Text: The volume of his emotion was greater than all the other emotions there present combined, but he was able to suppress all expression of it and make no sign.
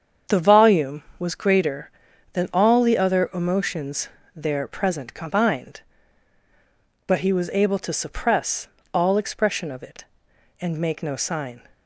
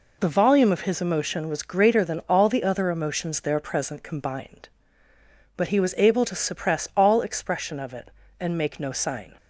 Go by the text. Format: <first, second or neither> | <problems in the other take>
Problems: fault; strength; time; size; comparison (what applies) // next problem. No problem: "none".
second | starts louder than the rest; strong; until 1.4 s; 7.5 dB // skips "of his emotion"; at 1.1 s // pauses between "emotions" and "there"; slight; at 4.0 s; 0.26 s long // pauses between "suppress" and "all"; slight; at 8.6 s; 0.26 s long